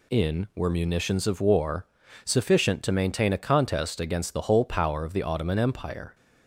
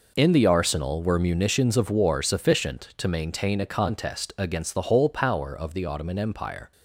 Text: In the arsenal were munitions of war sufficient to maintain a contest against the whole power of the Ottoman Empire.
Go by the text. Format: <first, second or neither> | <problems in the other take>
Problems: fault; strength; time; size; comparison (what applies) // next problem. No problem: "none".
second | skips "the arsenal"; at 0.5 s // pauses between "war" and "sufficient"; at 1.8 s; 0.38 s long